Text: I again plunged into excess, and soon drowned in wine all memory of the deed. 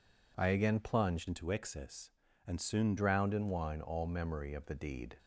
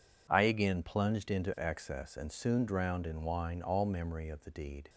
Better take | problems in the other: second | changes voice from "into" to "soon"; from 1.2 to 2.9 s; 1.7 s long

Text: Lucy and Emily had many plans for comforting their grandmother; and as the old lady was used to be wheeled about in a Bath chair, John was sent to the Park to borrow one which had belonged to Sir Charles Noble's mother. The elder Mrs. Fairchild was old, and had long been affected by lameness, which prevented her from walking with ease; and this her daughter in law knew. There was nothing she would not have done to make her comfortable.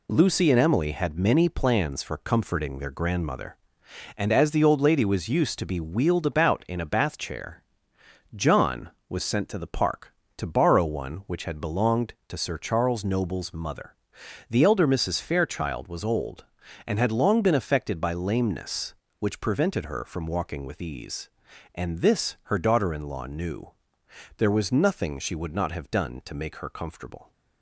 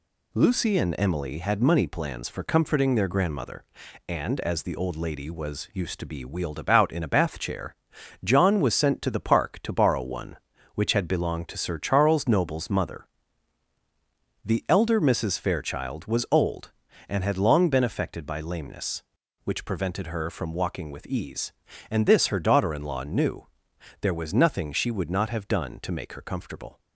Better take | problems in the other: first | says "money" for "many"; at 1.6 s

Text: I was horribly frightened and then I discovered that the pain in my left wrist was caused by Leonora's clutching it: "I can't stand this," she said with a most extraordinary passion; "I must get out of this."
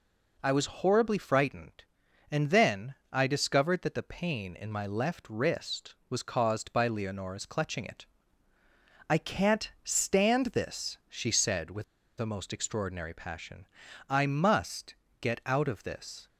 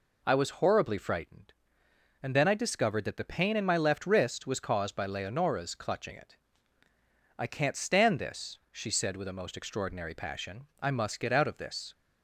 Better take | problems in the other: second | pauses between "then" and "I"; slight; at 2.9 s; 0.18 s long // pauses between "with" and "a"; slight; at 11.8 s; 0.36 s long // pauses between "must" and "get"; slight; at 14.9 s; 0.24 s long

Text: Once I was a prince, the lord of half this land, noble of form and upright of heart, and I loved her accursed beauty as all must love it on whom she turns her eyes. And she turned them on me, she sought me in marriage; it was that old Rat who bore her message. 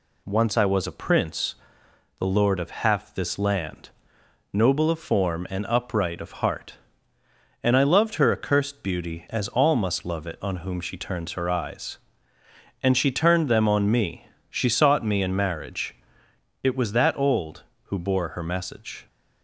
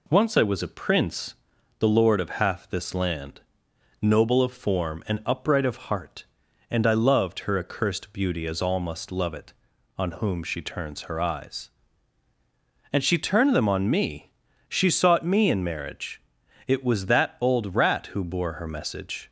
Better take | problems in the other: second | skips "Rat"; at 17.7 s

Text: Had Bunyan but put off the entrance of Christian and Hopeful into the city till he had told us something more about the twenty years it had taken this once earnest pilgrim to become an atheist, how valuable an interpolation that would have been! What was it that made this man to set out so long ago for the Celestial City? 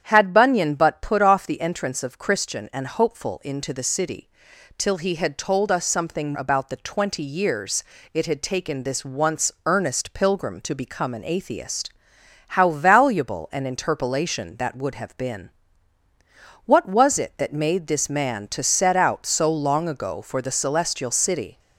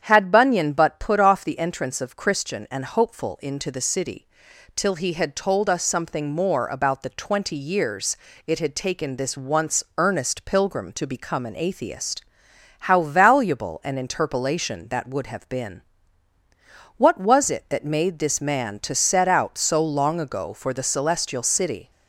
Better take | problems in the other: second | starts louder than the rest; strong; until 1.0 s; 9 dB; strong in the second // pauses between "city" and "till"; noticeable; at 4.2 s; 0.48 s long; noticeable in the second // skips "more"; at 6.3 s // pauses between "years" and "it"; slight; at 7.8 s; 0.30 s long; slight in the second

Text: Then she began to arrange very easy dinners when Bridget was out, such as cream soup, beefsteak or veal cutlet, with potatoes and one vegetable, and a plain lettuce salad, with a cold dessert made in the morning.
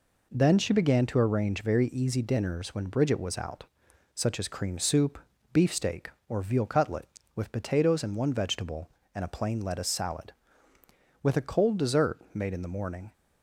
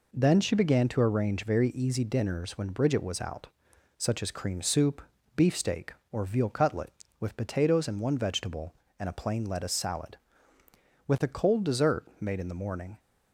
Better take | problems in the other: neither | none

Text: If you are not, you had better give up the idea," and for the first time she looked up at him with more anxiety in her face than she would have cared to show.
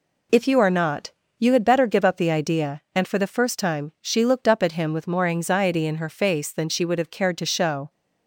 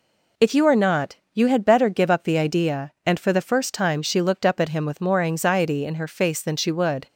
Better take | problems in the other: first | stops before "have cared to show"; at 7.0 s

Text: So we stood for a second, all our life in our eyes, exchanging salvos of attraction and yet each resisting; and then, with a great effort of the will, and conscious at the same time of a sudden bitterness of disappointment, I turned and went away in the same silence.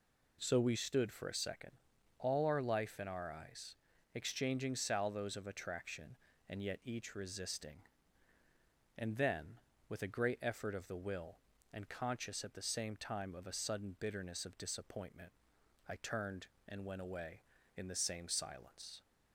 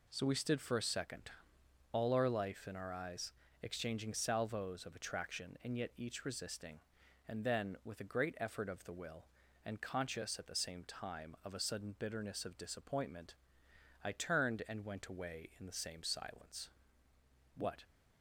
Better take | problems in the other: first | goes on to say "What"; slight; from 17.5 s on; 0.28 s long

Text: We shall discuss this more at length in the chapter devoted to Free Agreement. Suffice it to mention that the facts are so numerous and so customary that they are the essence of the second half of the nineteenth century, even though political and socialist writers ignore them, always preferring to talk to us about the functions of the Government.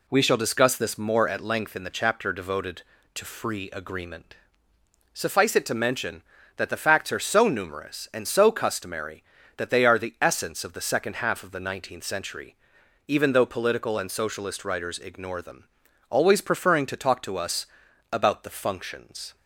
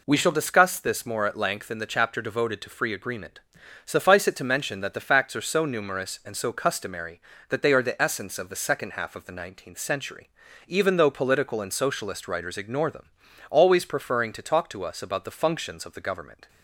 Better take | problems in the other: second | pauses between "us" and "about"; noticeable; at 17.6 s; 0.46 s long // stops before "of the Government"; at 19.3 s

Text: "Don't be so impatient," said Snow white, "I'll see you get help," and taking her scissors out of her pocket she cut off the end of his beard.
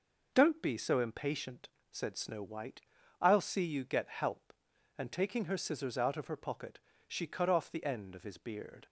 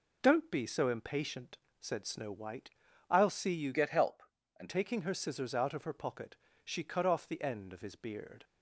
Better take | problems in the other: first | changes voice from "get" to "and"; from 3.7 to 4.6 s; 0.9 s long // pauses between "pocket" and "she"; slight; at 6.3 s; 0.30 s long; slight in the first

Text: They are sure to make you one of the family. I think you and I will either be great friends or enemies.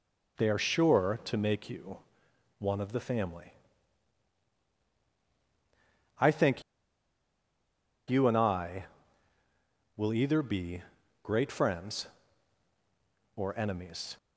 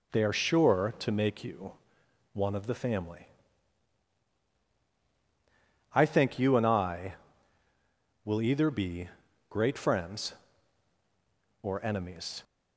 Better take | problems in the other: second | pauses between "you" and "one"; noticeable; at 1.9 s; 0.62 s long; noticeable in the second // pauses between "think" and "you"; strong; at 6.6 s; 1.4 s long // pauses between "be" and "great"; at 10.8 s; 0.42 s long; also in the second

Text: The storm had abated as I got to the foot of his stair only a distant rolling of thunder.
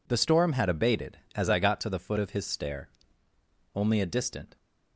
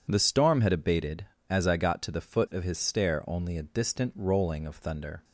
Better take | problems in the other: second | pauses between "stair" and "only"; noticeable; at 2.8 s; 0.86 s long // stops before "rolling of thunder"; at 4.5 s

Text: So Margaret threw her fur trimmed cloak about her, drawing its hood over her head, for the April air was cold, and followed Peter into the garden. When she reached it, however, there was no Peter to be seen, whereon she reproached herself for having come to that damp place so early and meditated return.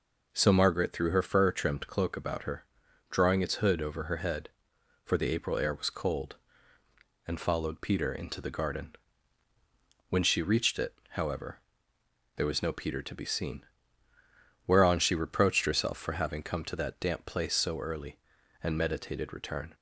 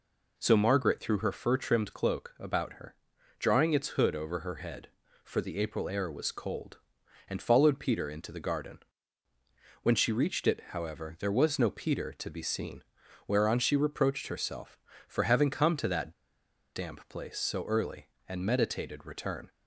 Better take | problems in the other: first | pauses between "that" and "damp"; noticeable; at 16.1 s; 0.63 s long

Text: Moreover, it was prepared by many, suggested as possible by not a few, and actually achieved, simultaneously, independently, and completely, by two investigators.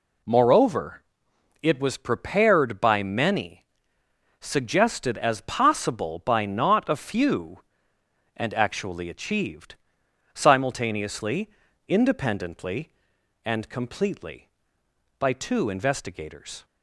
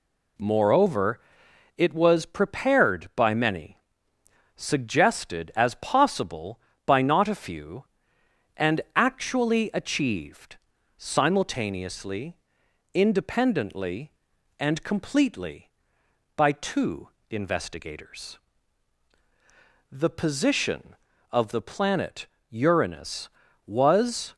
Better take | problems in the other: first | pauses between "two" and "investigators"; slight; at 17.0 s; 0.22 s long // goes on to say "The position of the planet Uranus was"; strong; from 19.9 s on; 4.4 s long

